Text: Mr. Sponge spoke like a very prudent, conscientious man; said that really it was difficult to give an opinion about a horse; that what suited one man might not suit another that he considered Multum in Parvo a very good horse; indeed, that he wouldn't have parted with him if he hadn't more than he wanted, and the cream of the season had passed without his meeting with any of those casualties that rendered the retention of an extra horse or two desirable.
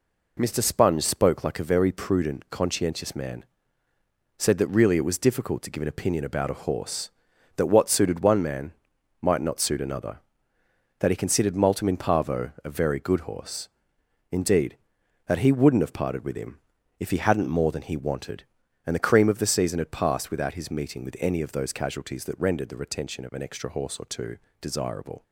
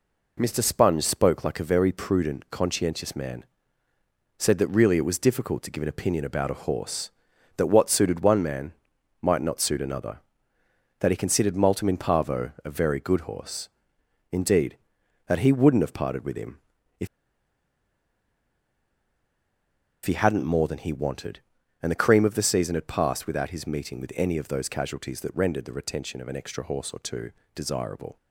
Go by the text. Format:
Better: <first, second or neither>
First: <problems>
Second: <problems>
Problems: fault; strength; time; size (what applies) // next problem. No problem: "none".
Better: first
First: pauses between "man" and "might"; noticeable; at 8.7 s; 0.48 s long // pauses between "him" and "if"; at 16.6 s; 0.40 s long // pauses between "two" and "desirable"; slight; at 24.3 s; 0.24 s long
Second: pauses between "man" and "might"; noticeable; at 8.7 s; 0.48 s long // pauses between "him" and "if"; at 16.6 s; 0.40 s long // pauses between "if" and "he"; strong; at 17.0 s; 2.9 s long // pauses between "two" and "desirable"; slight; at 27.3 s; 0.24 s long